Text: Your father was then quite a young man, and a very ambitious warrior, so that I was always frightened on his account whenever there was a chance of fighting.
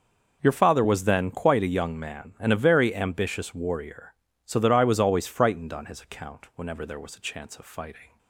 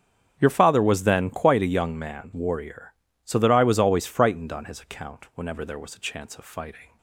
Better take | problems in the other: first | starts louder than the rest; strong; until 1.3 s; 8 dB // skips "and a very ambitious"; at 2.3 s

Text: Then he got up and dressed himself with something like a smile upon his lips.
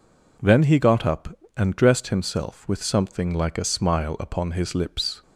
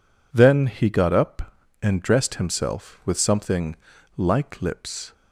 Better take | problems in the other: first | pauses between "something" and "like"; at 3.7 s; 0.42 s long // skips "a smile upon his"; at 4.6 s

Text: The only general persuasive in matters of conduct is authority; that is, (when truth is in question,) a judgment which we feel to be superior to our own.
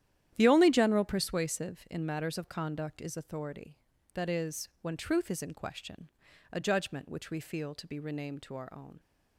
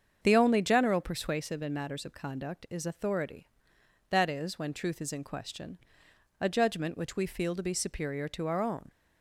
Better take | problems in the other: second | starts louder than the rest; strong; until 1.3 s; 11 dB; strong in the second // says "renamed" for "superior"; at 7.9 s

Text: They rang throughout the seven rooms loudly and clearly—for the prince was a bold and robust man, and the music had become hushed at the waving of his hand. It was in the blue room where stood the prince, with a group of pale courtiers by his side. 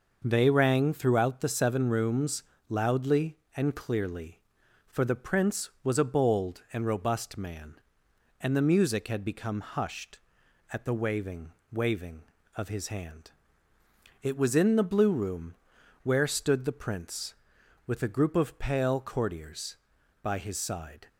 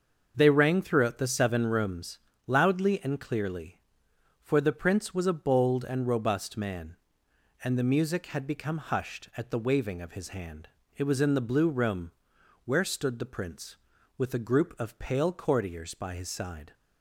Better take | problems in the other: second | starts louder than the rest; noticeable; until 1.2 s; 6 dB; also in the second // pauses between "rooms" and "loudly"; slight; at 2.4 s; 0.26 s long; slight in the second // says "waving" twice; at 11.7 s // pauses between "room" and "where"; noticeable; at 15.5 s; 0.48 s long; noticeable in the second

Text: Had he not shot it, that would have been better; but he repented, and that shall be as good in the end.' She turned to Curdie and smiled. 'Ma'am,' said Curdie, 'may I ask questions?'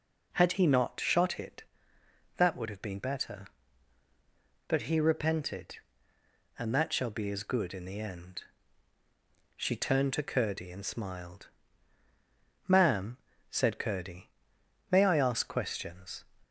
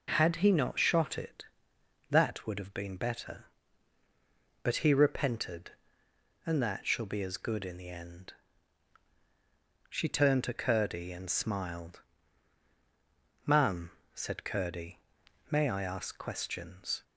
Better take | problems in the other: neither | none

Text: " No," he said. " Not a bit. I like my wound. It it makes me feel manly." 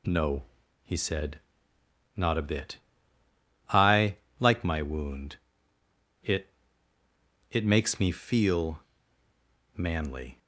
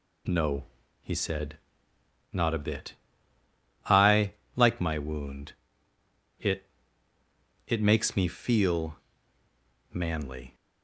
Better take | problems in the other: neither | pauses between "I" and "like"; slight; the same in both // pauses between "It" and "it"; the same in both // pauses between "feel" and "manly"; noticeable; the same in both

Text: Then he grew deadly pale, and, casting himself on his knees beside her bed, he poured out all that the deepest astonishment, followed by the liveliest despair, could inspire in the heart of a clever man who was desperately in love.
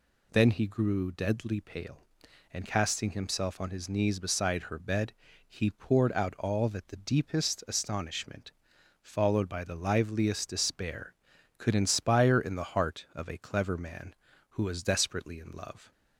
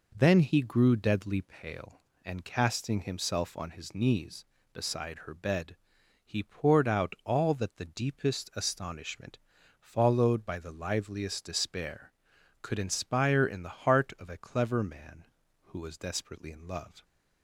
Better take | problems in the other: neither | none

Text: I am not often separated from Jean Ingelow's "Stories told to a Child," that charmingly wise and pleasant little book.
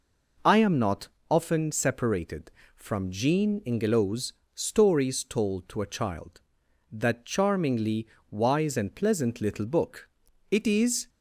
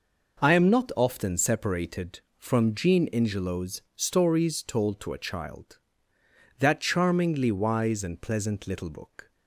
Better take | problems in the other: second | pauses between "not" and "often"; slight; at 1.0 s; 0.20 s long // pauses between "Ingelow's" and "Stories"; slight; at 4.3 s; 0.22 s long // pauses between "charmingly" and "wise"; slight; at 8.0 s; 0.24 s long // goes on to say "It is"; from 10.4 s on; 0.60 s long

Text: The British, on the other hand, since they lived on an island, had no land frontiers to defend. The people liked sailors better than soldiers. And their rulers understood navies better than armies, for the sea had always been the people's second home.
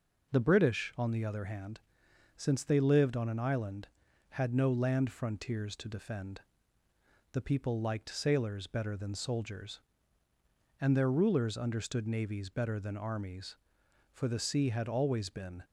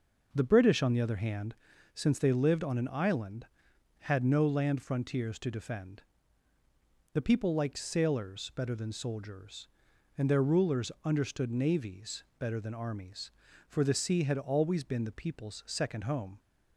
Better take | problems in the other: second | stops before "the people's second home"; at 15.6 s

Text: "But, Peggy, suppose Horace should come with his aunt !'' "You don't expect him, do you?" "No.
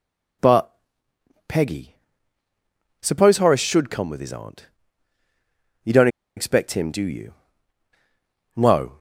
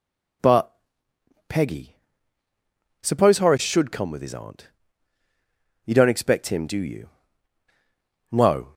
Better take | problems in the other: second | pauses between "don't" and "expect"; slight; at 6.0 s; 0.28 s long

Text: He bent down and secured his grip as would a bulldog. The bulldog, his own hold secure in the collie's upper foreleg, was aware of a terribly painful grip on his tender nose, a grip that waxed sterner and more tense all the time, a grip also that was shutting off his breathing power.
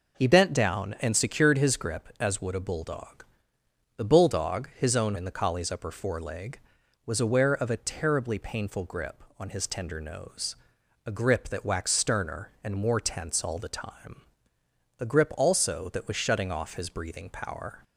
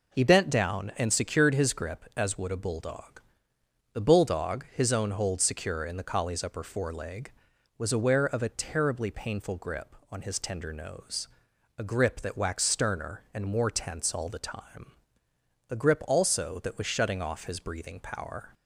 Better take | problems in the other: second | skips "hold secure"; at 5.1 s

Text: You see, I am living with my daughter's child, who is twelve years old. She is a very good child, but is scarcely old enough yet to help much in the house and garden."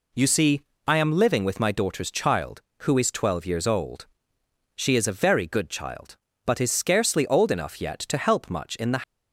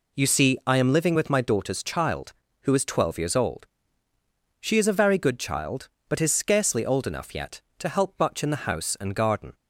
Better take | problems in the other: second | stops before "house and garden"; at 9.0 s

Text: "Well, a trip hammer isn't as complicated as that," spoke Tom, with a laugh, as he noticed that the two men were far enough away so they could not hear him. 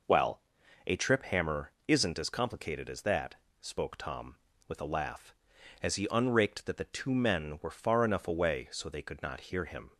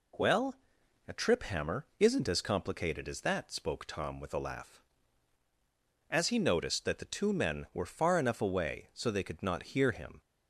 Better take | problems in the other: second | pauses between "hammer" and "isn't"; slight; at 1.7 s; 0.16 s long // says "unraked" for "noticed"; at 6.0 s

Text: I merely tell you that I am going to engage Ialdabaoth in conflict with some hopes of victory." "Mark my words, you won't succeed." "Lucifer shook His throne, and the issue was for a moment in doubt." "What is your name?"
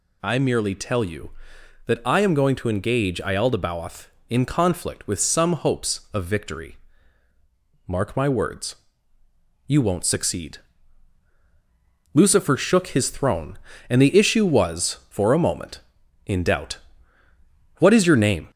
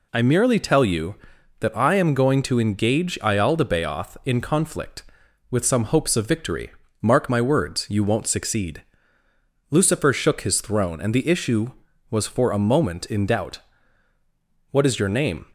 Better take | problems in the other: second | gets louder; slight; throughout; 2 dB

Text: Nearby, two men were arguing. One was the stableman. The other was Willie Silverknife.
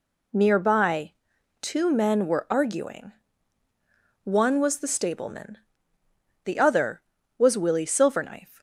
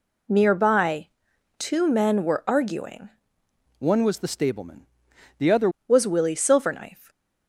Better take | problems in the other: first | changes voice from "One" to "other"; from 3.7 to 5.6 s; 1.9 s long

